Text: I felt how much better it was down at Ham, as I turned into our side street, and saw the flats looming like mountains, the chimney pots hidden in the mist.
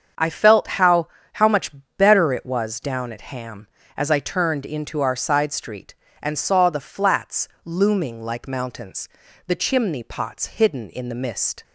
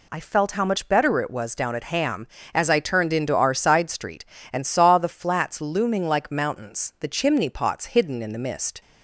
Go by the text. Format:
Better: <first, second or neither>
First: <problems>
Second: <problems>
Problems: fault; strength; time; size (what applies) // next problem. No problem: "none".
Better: second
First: starts louder than the rest; strong; until 1.5 s; 7 dB // says "how" twice; at 1.3 s // pauses between "much" and "better"; slight; at 1.7 s; 0.26 s long // pauses between "flats" and "looming"; slight; at 7.4 s; 0.18 s long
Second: none